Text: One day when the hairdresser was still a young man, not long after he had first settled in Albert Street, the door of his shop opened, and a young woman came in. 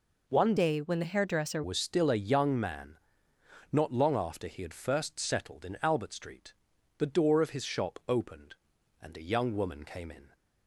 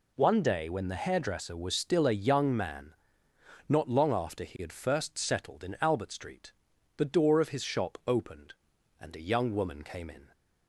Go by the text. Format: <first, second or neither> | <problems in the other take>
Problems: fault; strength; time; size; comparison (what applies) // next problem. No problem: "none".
second | changes voice from "day" to "hairdresser"; from 0.5 to 1.6 s; 1.1 s long